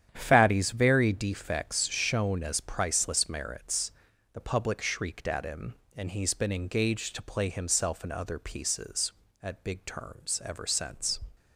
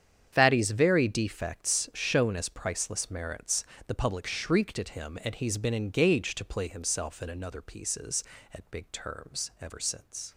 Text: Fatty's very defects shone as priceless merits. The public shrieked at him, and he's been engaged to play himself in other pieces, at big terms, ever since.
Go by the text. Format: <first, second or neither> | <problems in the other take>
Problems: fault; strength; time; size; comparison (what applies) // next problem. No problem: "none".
first | starts louder than the rest; strong; until 1.3 s; 8.5 dB; strong in the first // says "another" for "other"; at 7.2 s